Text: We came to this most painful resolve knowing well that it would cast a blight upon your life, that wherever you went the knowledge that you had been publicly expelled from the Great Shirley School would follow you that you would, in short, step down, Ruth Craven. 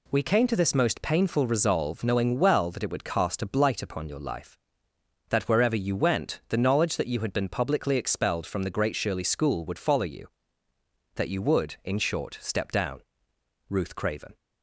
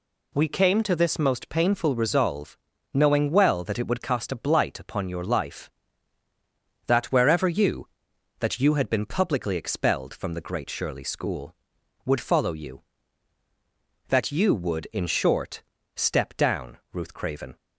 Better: first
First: none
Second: pauses between "resolve" and "knowing"; at 2.5 s; 0.38 s long // skips "went the knowledge"; at 8.1 s

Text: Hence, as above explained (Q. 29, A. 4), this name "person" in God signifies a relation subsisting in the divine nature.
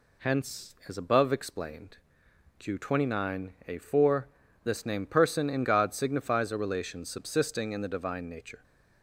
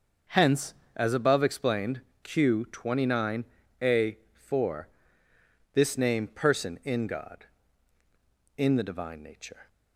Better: first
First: none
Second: starts louder than the rest; until 1.4 s; 6.5 dB // skips "signifies a relation subsisting"; at 8.0 s

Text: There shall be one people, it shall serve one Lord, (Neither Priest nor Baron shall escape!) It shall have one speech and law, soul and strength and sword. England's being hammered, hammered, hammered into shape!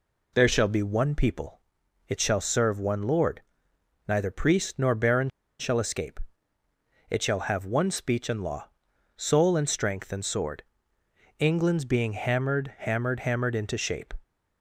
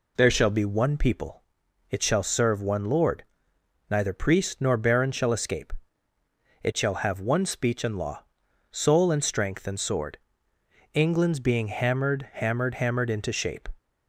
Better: second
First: pauses between "Baron" and "shall"; slight; at 5.2 s; 0.30 s long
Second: none

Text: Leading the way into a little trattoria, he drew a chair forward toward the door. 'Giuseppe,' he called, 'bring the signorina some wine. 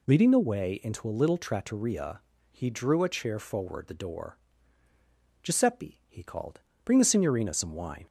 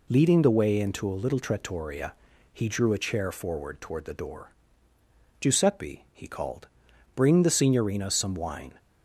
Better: second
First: skips "toward"; at 3.8 s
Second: none

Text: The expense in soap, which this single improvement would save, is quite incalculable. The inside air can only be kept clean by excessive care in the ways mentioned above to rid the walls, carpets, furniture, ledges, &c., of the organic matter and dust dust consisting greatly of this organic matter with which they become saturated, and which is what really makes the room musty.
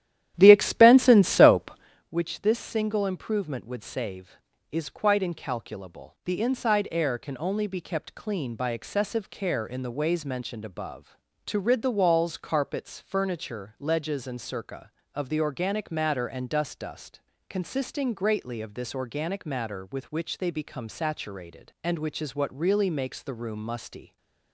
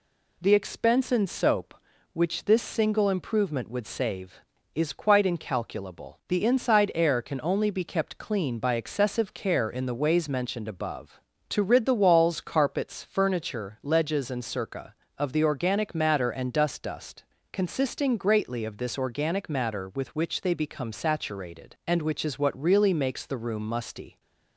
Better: second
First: starts louder than the rest; strong; until 2.1 s; 11.5 dB // pauses between "dust" and "consisting"; slight; at 17.2 s; 0.28 s long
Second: pauses between "dust" and "consisting"; slight; at 17.2 s; 0.28 s long

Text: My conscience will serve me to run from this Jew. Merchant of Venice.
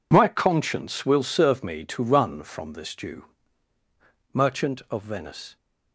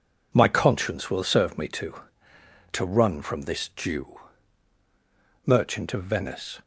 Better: first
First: none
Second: says "to" twice; at 2.7 s

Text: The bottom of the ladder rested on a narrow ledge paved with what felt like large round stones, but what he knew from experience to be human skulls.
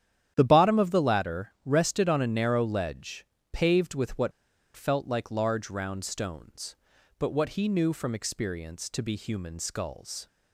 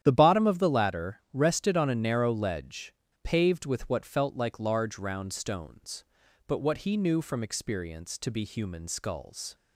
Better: second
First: starts louder than the rest; strong; until 1.3 s; 10.5 dB // pauses between "ledge" and "paved"; slight; at 3.2 s; 0.26 s long // pauses between "what" and "felt"; at 4.3 s; 0.45 s long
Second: starts louder than the rest; strong; until 1.0 s; 10.5 dB // pauses between "ledge" and "paved"; slight; at 2.9 s; 0.29 s long

